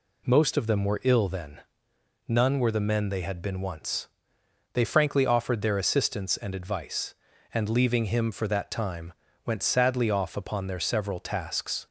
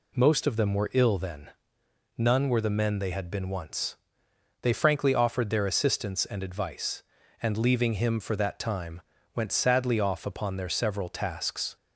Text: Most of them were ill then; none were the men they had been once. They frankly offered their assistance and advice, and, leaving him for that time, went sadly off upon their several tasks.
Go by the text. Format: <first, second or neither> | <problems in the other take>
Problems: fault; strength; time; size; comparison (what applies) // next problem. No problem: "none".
neither | none